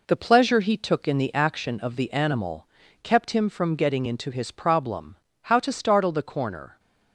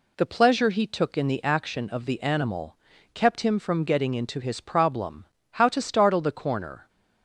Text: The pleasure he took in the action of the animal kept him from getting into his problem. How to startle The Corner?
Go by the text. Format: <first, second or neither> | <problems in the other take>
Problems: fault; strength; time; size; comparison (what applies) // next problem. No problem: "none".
second | gets quieter; noticeable; throughout; 5 dB // pauses between "animal" and "kept"; at 2.6 s; 0.37 s long; also in the second